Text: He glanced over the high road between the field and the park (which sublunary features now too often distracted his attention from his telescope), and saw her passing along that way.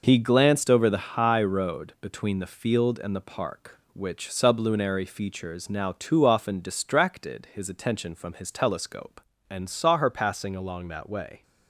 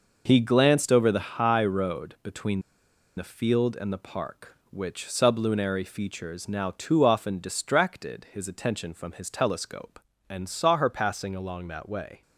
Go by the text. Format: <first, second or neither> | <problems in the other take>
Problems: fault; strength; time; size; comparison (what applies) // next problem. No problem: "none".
first | pauses between "between" and "the"; noticeable; at 2.6 s; 0.56 s long